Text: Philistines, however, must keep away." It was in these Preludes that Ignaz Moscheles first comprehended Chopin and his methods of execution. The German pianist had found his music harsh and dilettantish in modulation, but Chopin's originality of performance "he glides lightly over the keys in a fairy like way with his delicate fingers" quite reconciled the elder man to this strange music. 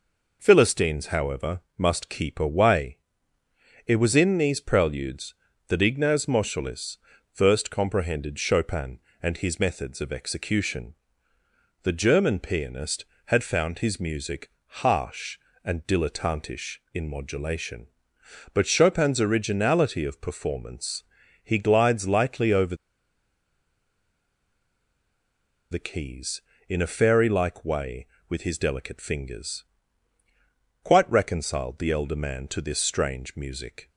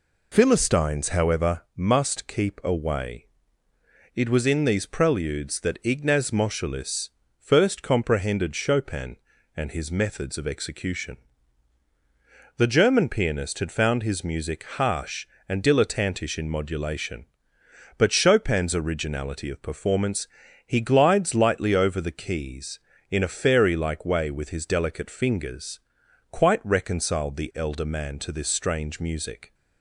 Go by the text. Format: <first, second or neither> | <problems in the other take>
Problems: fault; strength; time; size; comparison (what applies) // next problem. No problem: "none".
second | pauses between "Moscheles" and "first"; slight; at 6.9 s; 0.34 s long; slight in the second // pauses between "music" and "harsh"; slight; at 14.5 s; 0.16 s long // pauses between "performance" and "he"; at 21.0 s; 0.40 s long; also in the second // pauses between "over" and "the"; strong; at 22.7 s; 2.9 s long // pauses between "fingers" and "quite"; at 29.6 s; 1.1 s long; noticeable in the second